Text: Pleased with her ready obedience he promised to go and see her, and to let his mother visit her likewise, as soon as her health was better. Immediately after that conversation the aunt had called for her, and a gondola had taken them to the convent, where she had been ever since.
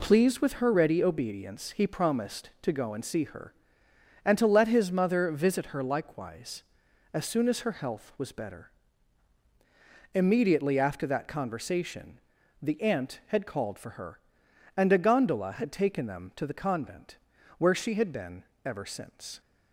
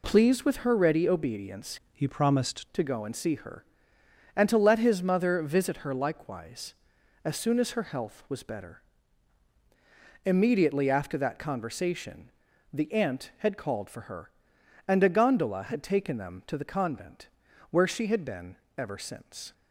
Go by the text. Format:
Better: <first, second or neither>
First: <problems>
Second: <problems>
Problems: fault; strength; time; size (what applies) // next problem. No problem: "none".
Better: first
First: pauses between "conversation" and "the"; at 12.1 s; 0.44 s long // pauses between "been" and "ever"; slight; at 18.4 s; 0.20 s long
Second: changes voice from "he" to "promised"; from 1.9 to 2.6 s; 0.7 s long // pauses between "conversation" and "the"; at 12.2 s; 0.44 s long // pauses between "been" and "ever"; slight; at 18.5 s; 0.20 s long